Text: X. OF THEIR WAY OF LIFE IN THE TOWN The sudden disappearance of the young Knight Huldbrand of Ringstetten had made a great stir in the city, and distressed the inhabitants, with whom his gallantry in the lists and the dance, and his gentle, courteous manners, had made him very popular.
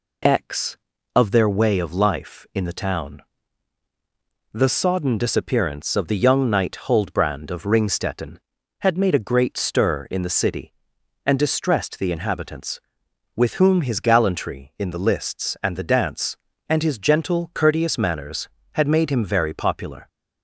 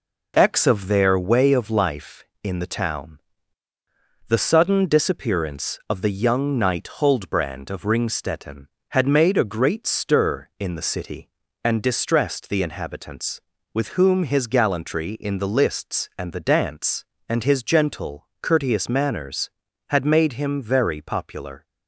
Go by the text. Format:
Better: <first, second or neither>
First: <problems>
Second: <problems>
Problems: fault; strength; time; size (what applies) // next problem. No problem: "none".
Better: second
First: pauses between "TOWN" and "The"; strong; at 3.2 s; 1.3 s long // says "sodden" for "sudden"; at 4.6 s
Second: pauses between "TOWN" and "The"; at 3.1 s; 1.0 s long